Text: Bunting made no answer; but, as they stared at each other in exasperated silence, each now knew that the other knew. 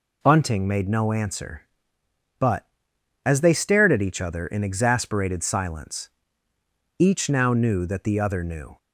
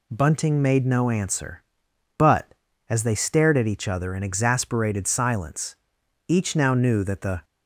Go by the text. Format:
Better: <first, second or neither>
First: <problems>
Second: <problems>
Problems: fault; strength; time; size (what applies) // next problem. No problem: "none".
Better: first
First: none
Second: stops before "other knew"; at 7.4 s